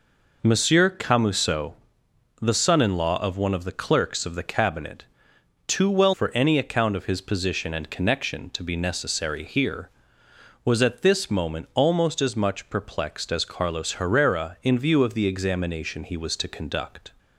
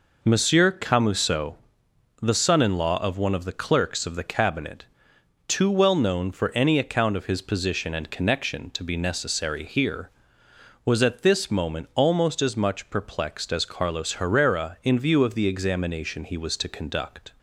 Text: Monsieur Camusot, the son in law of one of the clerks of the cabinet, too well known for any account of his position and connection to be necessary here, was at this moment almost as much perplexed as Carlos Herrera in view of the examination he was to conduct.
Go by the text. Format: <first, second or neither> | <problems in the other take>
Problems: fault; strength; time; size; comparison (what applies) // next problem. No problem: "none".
second | skips "known"; at 6.1 s